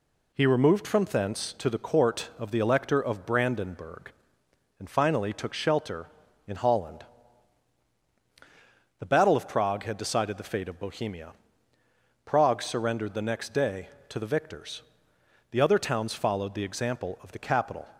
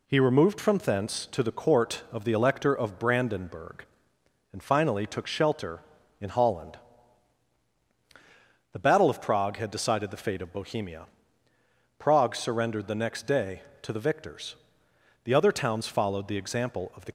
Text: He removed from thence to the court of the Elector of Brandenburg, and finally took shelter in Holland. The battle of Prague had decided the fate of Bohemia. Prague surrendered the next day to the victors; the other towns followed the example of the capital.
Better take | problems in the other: first | stops before "capital"; at 17.0 s

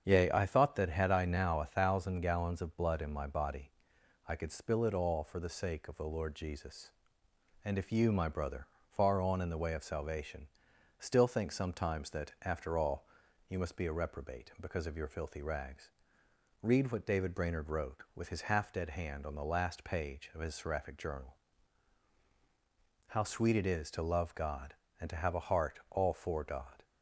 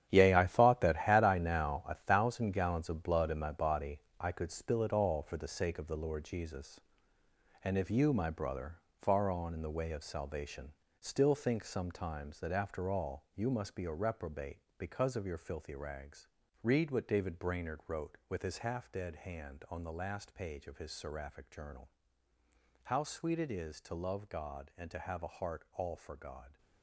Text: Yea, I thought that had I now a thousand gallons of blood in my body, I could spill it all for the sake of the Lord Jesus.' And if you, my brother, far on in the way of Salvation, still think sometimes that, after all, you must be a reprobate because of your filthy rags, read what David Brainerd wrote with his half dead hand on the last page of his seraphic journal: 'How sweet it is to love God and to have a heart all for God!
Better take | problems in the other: first | gets quieter; strong; throughout; 11.5 dB // starts louder than the rest; strong; until 1.1 s; 9.5 dB; strong in the first

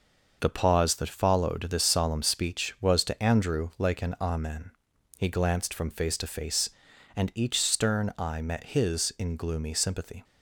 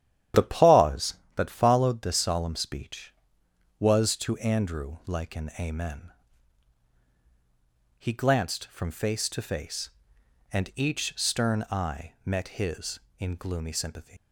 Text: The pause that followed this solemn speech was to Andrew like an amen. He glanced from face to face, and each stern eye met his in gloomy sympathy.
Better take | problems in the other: first | starts louder than the rest; strong; until 1.5 s; 11 dB // leaves "sympathy" unfinished; at 14.1 s; 65 ms

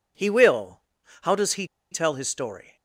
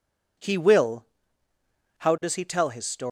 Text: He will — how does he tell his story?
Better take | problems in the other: second | pauses between "he" and "tell"; slight; at 1.6 s; 0.25 s long

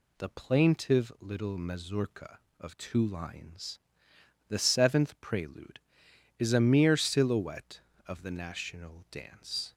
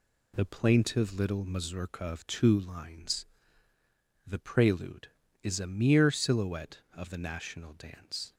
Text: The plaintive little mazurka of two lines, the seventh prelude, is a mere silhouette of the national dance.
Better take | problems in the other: first | skips "seventh"; at 4.3 s

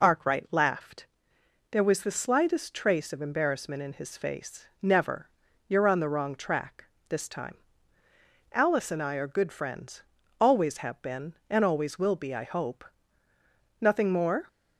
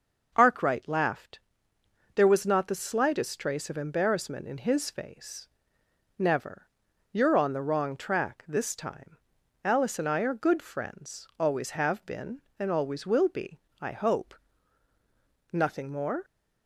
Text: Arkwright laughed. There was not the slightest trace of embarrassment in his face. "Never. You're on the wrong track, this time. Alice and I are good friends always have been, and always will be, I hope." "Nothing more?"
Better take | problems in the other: second | skips "not"; at 2.0 s // pauses between "friends" and "always"; at 10.0 s; 0.38 s long

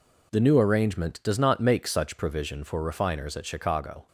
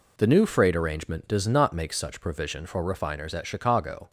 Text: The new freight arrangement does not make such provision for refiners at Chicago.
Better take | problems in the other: second | skips "freight"; at 0.5 s

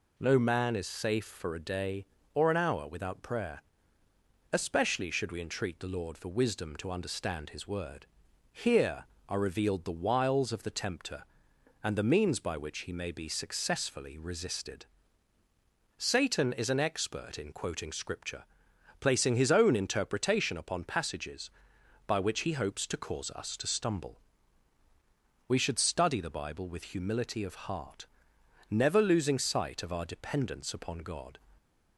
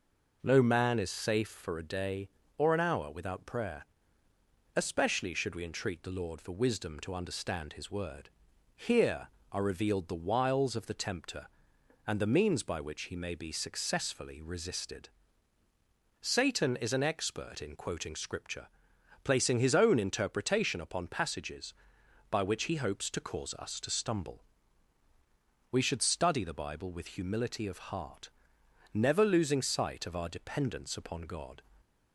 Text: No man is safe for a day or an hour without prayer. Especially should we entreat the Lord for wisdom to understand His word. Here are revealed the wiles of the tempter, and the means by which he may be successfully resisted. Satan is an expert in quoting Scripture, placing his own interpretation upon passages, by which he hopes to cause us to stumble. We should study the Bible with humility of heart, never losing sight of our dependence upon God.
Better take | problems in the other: first | starts louder than the rest; noticeable; until 1.5 s; 5.5 dB

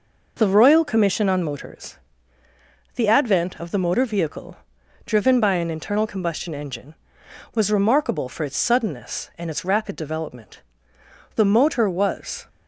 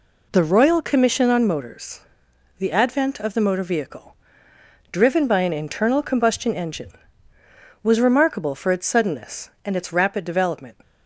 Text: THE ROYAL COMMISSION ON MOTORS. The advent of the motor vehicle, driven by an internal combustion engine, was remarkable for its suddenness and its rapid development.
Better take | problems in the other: second | goes on to say "The motor was"; noticeable; from 11.3 s on; 1.1 s long

